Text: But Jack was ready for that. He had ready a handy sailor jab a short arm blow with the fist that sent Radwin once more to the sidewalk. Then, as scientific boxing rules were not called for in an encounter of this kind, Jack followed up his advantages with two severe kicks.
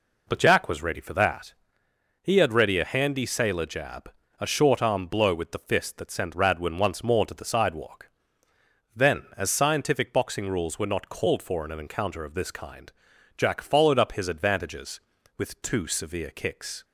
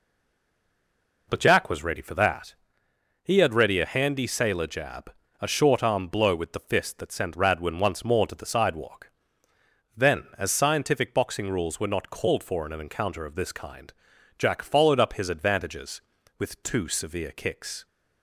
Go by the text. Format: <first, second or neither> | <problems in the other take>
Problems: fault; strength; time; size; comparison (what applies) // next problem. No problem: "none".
first | stays silent before the first word; noticeable; until 1.2 s; 1.2 s long // pauses between "jab" and "a"; slight; at 5.1 s; 0.30 s long; slight in the first